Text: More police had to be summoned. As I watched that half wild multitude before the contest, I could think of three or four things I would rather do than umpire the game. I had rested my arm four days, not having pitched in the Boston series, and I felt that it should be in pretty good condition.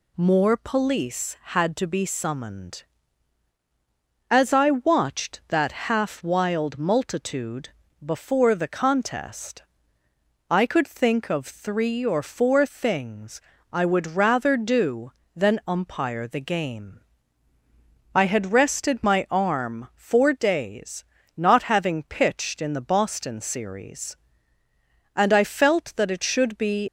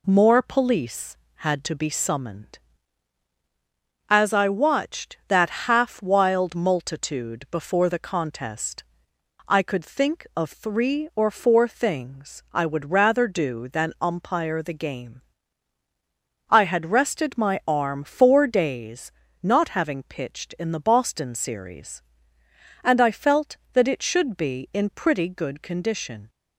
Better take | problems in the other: second | pauses between "multitude" and "before"; slight; at 7.6 s; 0.34 s long // pauses between "things" and "I"; slight; at 13.3 s; 0.32 s long // stops before "in pretty good condition"; at 26.8 s

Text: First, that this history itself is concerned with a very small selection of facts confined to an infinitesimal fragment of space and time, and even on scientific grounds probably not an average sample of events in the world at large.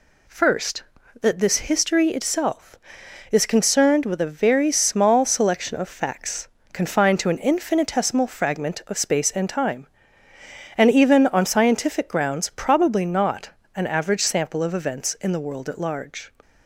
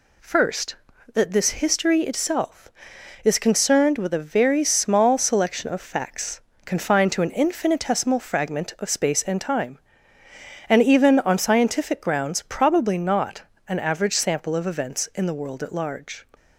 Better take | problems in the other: neither | pauses between "facts" and "confined"; slight; the same in both // pauses between "not" and "an"; slight; the same in both

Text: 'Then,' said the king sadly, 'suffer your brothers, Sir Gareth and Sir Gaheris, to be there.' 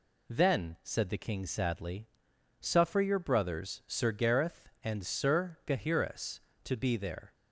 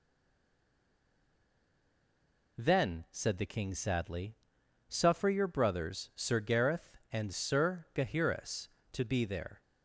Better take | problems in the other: first | stays silent before the first word; strong; until 2.5 s; 2.5 s long

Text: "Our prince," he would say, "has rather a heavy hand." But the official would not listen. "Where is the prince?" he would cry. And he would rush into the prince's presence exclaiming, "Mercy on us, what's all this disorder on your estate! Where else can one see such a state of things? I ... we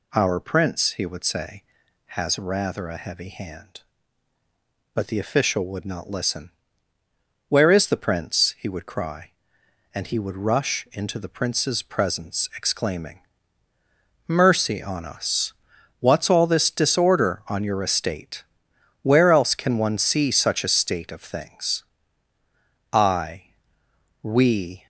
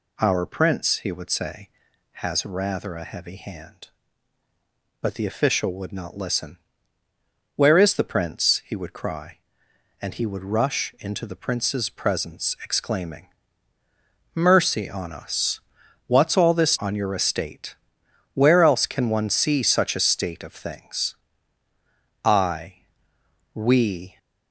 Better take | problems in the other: first | skips "disorder"; at 16.7 s

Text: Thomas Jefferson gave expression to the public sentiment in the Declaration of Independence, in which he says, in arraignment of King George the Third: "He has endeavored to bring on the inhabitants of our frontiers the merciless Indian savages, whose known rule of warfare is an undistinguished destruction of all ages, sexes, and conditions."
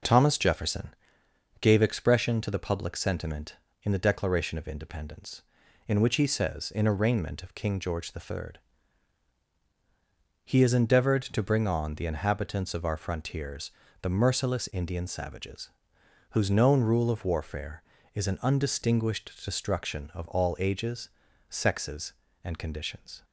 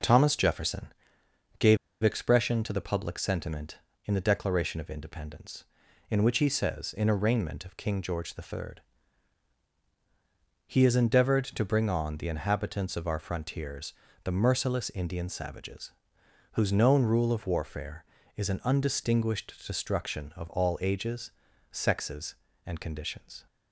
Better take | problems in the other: first | pauses between "Jefferson" and "gave"; noticeable; at 0.8 s; 0.72 s long; noticeable in the first // pauses between "gave" and "expression"; slight; at 1.7 s; 0.26 s long // pauses between "frontiers" and "the"; slight; at 13.9 s; 0.30 s long; slight in the first

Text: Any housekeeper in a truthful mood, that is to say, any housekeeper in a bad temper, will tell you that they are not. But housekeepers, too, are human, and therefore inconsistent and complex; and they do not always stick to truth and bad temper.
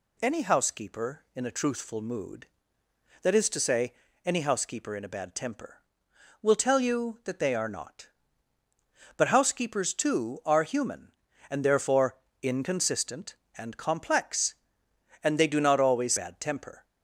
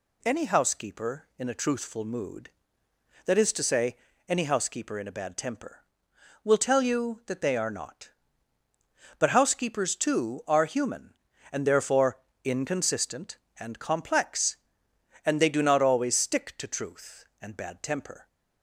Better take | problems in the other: second | pauses between "therefore" and "inconsistent"; slight; at 12.1 s; 0.26 s long; slight in the second // skips "stick to truth and"; at 16.1 s

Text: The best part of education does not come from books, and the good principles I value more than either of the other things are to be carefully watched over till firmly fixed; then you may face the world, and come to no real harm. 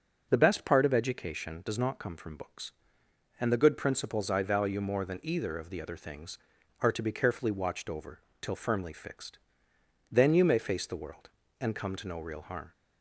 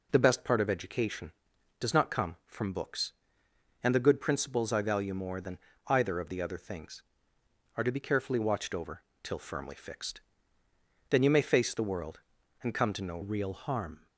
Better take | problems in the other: first | pauses between "than" and "either"; slight; at 5.5 s; 0.26 s long // pauses between "over" and "till"; slight; at 9.0 s; 0.20 s long; slight in the first // changes voice at "real"; from 13.2 s on; 0.8 s long

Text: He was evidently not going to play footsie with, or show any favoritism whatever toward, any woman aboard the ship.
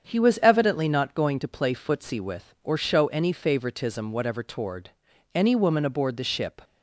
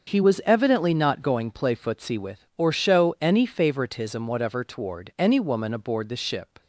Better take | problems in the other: first | starts louder than the rest; until 1.1 s; 6.5 dB; strong in the first // skips "to"; at 1.5 s

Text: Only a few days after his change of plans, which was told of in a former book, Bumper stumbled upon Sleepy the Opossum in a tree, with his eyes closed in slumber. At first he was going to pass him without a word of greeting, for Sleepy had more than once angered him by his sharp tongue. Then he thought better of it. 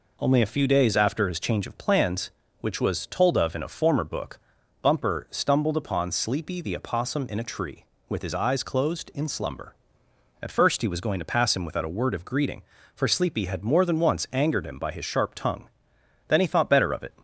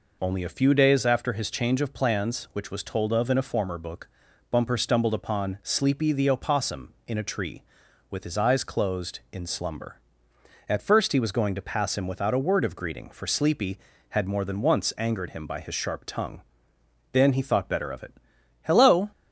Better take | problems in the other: first | goes on to say "Hello"; slight; from 18.6 s on; 0.48 s long

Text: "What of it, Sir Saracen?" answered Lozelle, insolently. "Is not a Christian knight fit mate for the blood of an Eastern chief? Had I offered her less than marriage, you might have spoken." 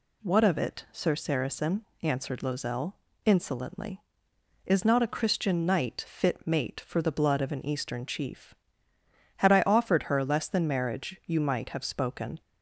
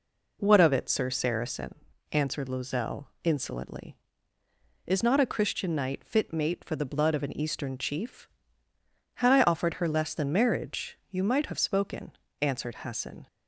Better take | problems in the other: first | goes on to say "answered Hassan"; noticeable; from 12.4 s on; 0.86 s long

